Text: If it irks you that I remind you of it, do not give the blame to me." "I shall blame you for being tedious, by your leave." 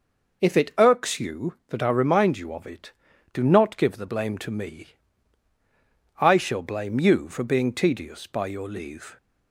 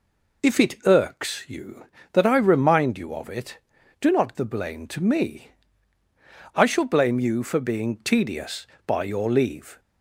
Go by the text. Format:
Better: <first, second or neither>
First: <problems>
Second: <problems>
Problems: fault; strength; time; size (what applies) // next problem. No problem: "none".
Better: first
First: none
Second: skips "give"; at 4.3 s